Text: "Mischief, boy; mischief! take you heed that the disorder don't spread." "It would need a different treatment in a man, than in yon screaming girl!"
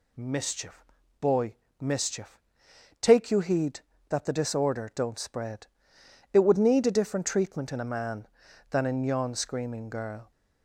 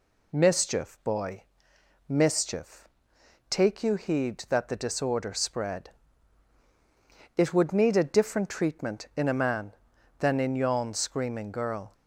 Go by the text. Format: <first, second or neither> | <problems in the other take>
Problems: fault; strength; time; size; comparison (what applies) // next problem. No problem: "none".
first | skips "don't"; at 5.3 s